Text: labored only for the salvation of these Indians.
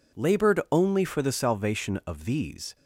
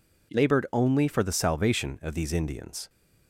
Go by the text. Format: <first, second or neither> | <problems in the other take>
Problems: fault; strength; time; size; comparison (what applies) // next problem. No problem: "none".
second | stops before "Indians"; at 2.7 s